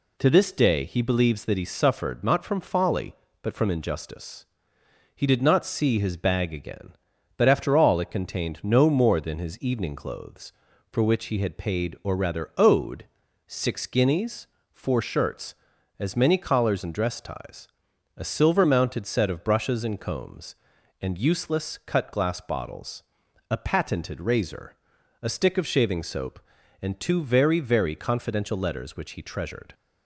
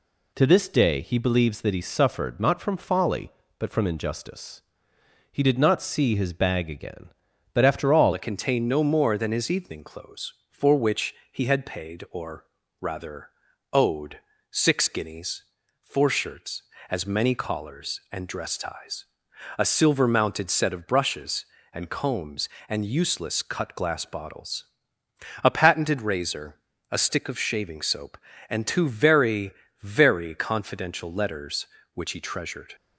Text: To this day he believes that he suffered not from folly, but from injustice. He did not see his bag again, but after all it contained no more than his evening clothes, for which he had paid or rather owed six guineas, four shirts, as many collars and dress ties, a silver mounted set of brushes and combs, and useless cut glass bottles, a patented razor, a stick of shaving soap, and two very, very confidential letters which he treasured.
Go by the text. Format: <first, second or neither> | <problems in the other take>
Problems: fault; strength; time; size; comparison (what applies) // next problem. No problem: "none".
first | changes voice at "it"; from 8.1 s on; 24.6 s long // pauses between "which" and "he"; slight; at 11.1 s; 0.16 s long // pauses between "or" and "rather"; slight; at 12.4 s; 0.34 s long // pauses between "rather" and "owed"; at 13.2 s; 0.44 s long // pauses between "owed" and "six"; slight; at 14.1 s; 0.32 s long; also in the first